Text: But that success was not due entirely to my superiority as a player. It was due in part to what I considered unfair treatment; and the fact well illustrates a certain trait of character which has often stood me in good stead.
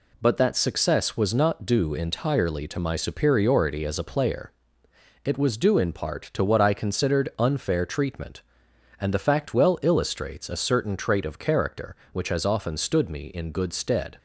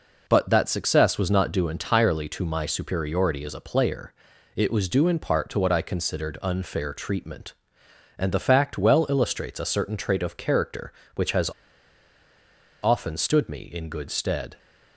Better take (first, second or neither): first